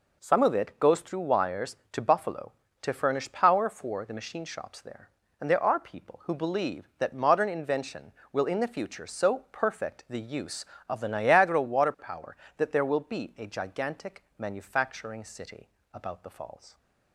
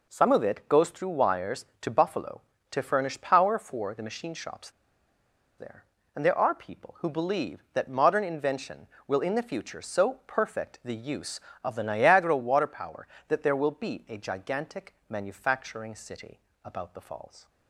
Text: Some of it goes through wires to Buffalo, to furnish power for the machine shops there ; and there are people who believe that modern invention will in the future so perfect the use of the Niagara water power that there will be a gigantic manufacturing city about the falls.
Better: first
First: pauses between "city" and "about"; slight; at 15.6 s; 0.26 s long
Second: pauses between "shops" and "there"; noticeable; at 4.7 s; 0.87 s long // pauses between "city" and "about"; slight; at 16.3 s; 0.26 s long

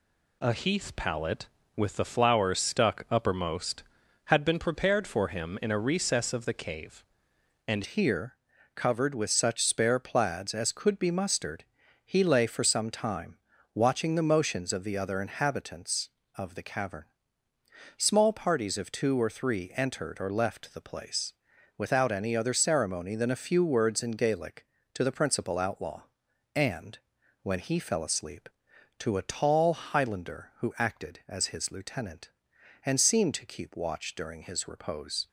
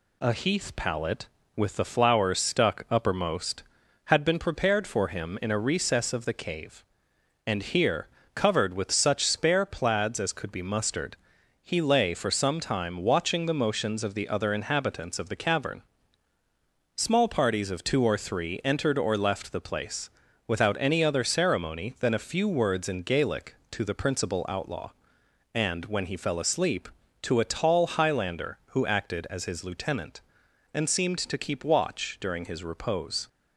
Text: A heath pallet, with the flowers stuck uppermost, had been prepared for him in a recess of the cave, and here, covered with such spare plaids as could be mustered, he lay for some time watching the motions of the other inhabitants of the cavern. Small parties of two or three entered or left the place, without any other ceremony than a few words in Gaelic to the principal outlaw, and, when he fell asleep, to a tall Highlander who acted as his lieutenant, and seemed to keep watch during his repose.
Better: second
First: changes voice at "here"; from 7.8 s on; 27.4 s long // pauses between "time" and "watching"; slight; at 13.3 s; 0.36 s long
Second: none

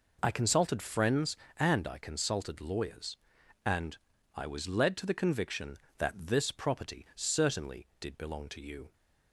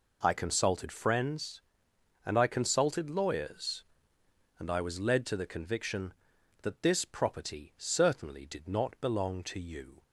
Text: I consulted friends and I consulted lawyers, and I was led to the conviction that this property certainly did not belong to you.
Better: second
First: pauses between "and" and "I"; at 3.9 s; 0.40 s long // skips "not"; at 8.1 s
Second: none

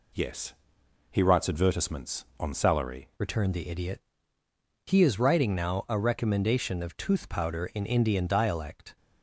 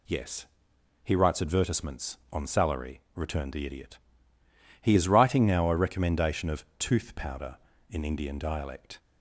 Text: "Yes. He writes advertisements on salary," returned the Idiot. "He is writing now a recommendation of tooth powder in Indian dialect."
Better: second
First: changes voice at "returned"; from 3.1 s on; 5.8 s long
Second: none

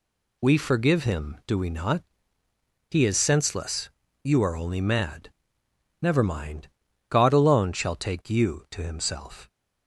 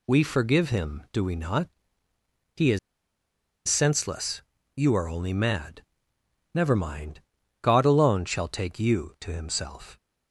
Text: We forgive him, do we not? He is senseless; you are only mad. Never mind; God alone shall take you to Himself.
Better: first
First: none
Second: pauses between "is" and "senseless"; noticeable; at 2.7 s; 0.89 s long

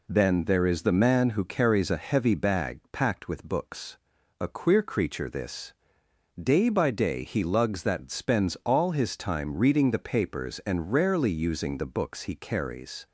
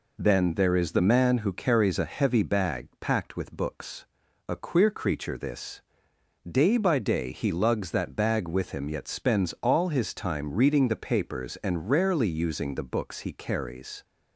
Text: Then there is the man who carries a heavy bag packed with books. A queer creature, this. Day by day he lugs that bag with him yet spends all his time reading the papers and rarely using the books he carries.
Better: second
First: skips "bag with him yet"; at 8.0 s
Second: none

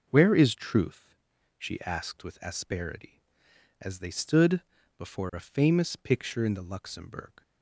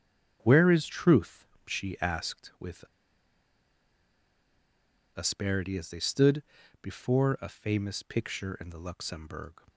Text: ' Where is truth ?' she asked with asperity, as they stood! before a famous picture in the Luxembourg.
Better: first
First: none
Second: starts louder than the rest; strong; until 1.4 s; 7.5 dB // pauses between "with" and "asperity"; strong; at 2.8 s; 2.3 s long

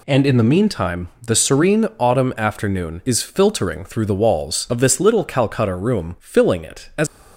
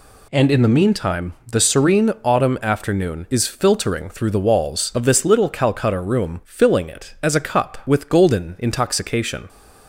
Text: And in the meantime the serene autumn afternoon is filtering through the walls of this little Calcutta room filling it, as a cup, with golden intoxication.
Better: second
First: stops before "a cup with golden intoxication"; at 7.0 s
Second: none

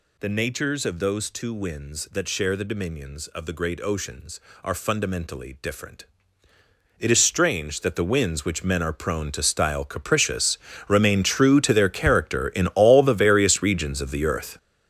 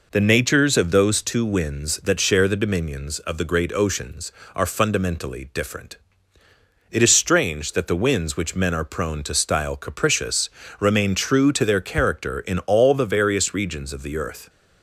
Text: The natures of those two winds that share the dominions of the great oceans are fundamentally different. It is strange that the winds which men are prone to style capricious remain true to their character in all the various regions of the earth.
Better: second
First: gets louder; strong; throughout; 10.5 dB // pauses between "capricious" and "remain"; slight; at 10.5 s; 0.30 s long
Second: pauses between "capricious" and "remain"; slight; at 10.4 s; 0.30 s long

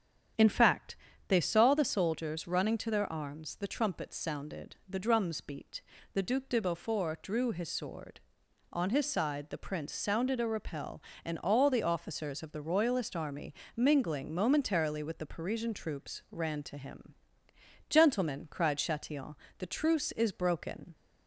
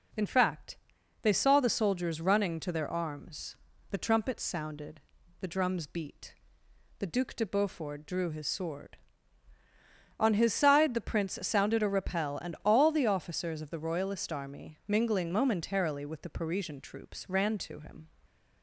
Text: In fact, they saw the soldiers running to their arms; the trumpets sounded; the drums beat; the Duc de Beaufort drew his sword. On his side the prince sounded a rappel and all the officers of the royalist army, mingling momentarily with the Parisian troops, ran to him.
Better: second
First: starts louder than the rest; strong; until 1.6 s; 8.5 dB // goes on to say "Gentlemen cried Chatillon the truce is broken"; strong; from 17.8 s on; 3.0 s long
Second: none

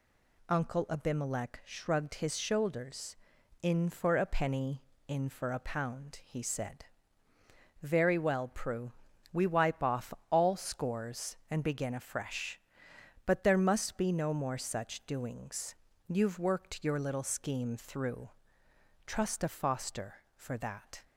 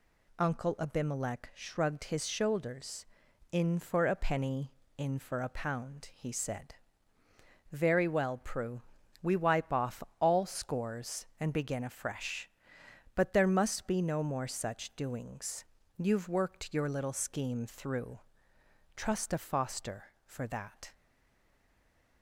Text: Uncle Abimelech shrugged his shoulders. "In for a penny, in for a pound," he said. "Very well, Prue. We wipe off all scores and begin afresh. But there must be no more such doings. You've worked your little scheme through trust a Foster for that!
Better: first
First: pauses between "off" and "all"; slight; at 10.1 s; 0.16 s long // pauses between "through" and "trust"; noticeable; at 18.2 s; 0.76 s long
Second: pauses between "off" and "all"; slight; at 10.0 s; 0.16 s long // pauses between "through" and "trust"; noticeable; at 18.1 s; 0.76 s long // stays silent after the last word; noticeable; from 20.9 s on; 1.3 s long

